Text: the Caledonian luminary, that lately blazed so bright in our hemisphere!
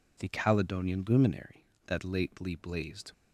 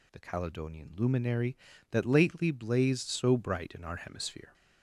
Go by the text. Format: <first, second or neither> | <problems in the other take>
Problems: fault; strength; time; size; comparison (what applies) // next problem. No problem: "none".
second | stops before "so bright in our hemisphere"; at 3.1 s